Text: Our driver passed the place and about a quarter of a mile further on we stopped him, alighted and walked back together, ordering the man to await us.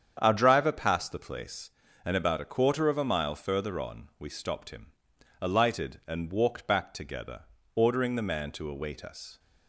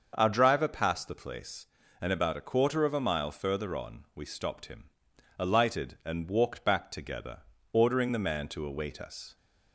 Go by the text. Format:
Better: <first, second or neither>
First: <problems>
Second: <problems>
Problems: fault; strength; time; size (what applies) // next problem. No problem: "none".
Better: second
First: gets quieter; strong; throughout; 7.5 dB // starts louder than the rest; strong; until 1.2 s; 8 dB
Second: starts louder than the rest; until 1.1 s; 6.5 dB